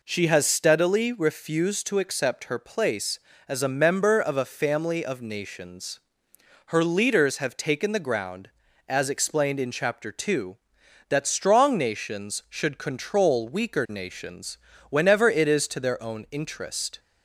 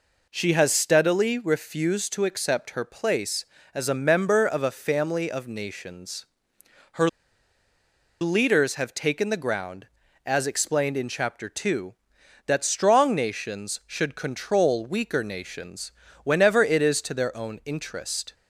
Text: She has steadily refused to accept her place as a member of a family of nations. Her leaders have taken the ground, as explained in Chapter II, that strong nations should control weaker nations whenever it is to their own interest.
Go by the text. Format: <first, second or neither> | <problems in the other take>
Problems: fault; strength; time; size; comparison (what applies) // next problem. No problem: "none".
first | pauses between "Her" and "leaders"; at 7.0 s; 1.1 s long // pauses between "nations" and "whenever"; slight; at 15.9 s; 0.34 s long; slight in the first